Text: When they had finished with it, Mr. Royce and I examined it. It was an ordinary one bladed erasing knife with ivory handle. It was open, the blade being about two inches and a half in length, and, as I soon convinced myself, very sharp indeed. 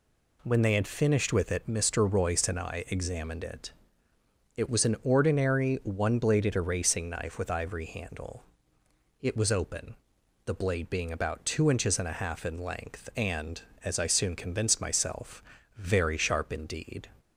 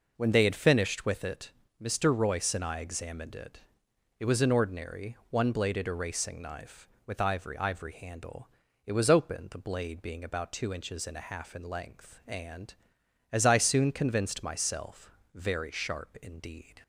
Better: first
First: none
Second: says "ivory" twice; at 7.5 s

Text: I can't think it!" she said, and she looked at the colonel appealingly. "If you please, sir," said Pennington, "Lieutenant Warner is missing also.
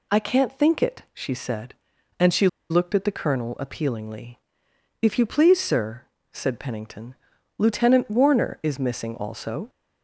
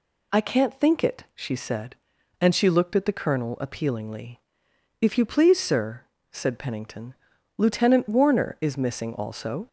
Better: second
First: pauses between "she" and "looked"; slight; at 2.4 s; 0.23 s long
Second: none

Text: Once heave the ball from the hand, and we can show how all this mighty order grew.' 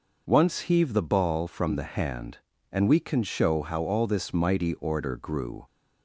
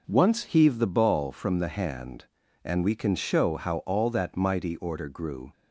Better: first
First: none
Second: says "that" for "this"; at 4.1 s

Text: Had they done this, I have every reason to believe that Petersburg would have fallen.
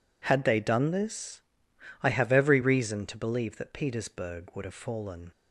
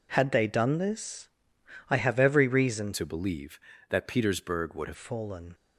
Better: first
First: none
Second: changes voice from "to" to "have"; from 2.9 to 4.9 s; 2.0 s long

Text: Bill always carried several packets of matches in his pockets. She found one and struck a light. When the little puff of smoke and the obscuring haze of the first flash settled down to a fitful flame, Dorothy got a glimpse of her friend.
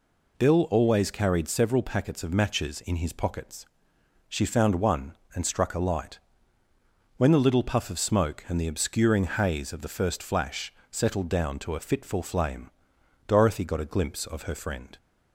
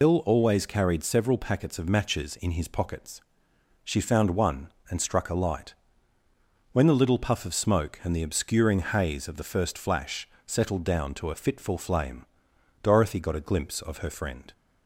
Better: first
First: pauses between "flash" and "settled"; slight; at 10.7 s; 0.18 s long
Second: loses the start of "Bill"; at 0.0 s; 90 ms // pauses between "flash" and "settled"; slight; at 10.2 s; 0.18 s long

